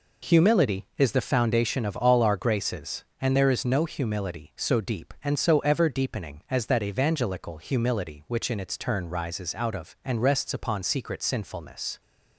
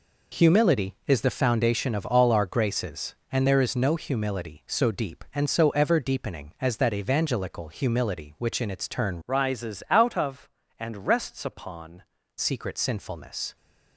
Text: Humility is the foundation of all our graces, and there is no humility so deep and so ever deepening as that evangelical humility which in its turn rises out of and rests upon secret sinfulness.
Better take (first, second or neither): first